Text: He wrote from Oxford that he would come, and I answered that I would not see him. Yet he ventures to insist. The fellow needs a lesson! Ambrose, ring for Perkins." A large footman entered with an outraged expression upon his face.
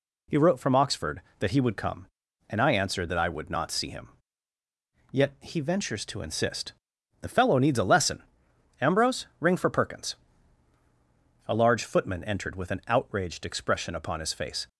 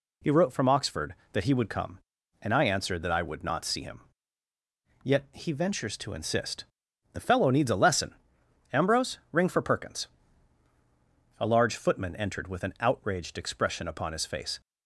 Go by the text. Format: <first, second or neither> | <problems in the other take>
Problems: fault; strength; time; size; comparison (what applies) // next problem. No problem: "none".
neither | none